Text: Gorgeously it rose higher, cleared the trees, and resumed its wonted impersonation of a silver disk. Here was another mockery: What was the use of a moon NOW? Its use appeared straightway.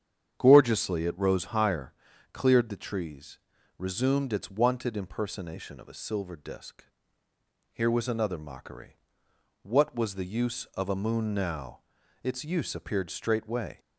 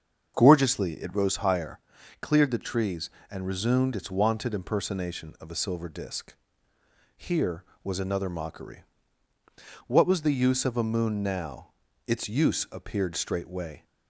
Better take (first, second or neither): second